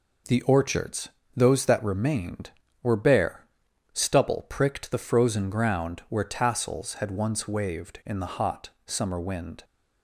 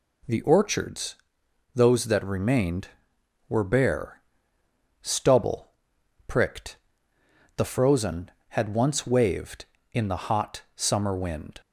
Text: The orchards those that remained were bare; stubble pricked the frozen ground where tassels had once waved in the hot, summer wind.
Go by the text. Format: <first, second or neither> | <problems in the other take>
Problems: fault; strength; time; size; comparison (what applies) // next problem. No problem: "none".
first | pauses between "orchards" and "those"; noticeable; at 1.1 s; 0.59 s long; slight in the first // pauses between "stubble" and "pricked"; noticeable; at 5.7 s; 0.56 s long // pauses between "pricked" and "the"; noticeable; at 6.7 s; 0.80 s long // skips "ground where tassels"; at 8.4 s